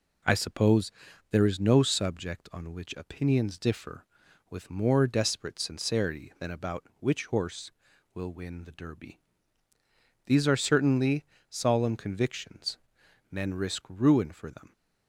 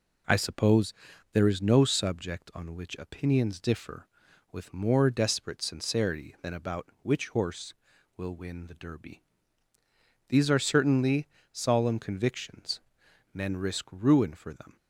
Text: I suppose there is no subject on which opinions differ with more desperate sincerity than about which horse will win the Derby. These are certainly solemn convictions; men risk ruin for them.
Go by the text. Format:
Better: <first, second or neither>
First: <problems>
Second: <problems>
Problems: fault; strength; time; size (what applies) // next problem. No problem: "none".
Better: neither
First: pauses between "suppose" and "there"; at 0.9 s; 0.40 s long // pauses between "certainly" and "solemn"; slight; at 11.2 s; 0.26 s long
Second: pauses between "suppose" and "there"; at 0.9 s; 0.40 s long // pauses between "certainly" and "solemn"; slight; at 11.2 s; 0.26 s long